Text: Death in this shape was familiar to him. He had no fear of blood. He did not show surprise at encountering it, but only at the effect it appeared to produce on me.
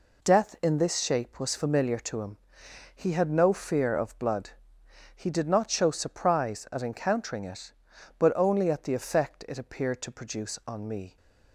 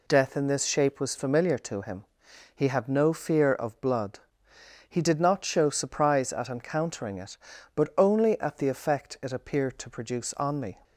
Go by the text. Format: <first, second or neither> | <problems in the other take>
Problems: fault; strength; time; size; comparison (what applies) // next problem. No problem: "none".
neither | none